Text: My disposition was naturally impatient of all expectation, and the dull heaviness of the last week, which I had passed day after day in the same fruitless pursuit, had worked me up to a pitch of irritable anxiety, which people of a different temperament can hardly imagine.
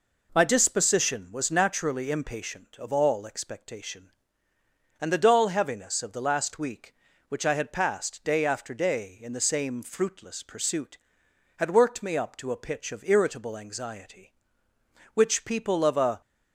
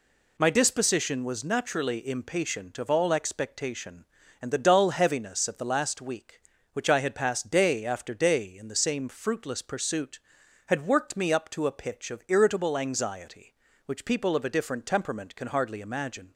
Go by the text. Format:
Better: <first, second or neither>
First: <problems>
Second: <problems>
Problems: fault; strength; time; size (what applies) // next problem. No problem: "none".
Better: second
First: stops before "different temperament can hardly imagine"; at 16.2 s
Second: none